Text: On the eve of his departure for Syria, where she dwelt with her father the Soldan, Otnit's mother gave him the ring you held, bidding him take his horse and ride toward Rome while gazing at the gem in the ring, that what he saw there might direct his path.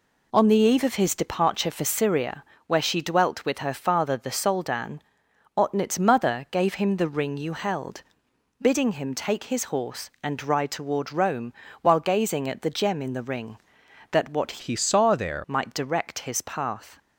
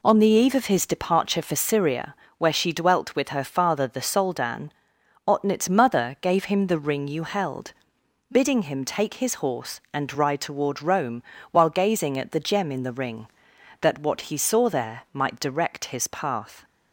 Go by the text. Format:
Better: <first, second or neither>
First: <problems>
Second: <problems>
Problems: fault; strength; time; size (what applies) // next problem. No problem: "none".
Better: second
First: pauses between "Rome" and "while"; slight; at 11.5 s; 0.30 s long // changes voice from "he" to "there"; from 14.6 to 15.4 s; 0.8 s long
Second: pauses between "Rome" and "while"; slight; at 11.2 s; 0.30 s long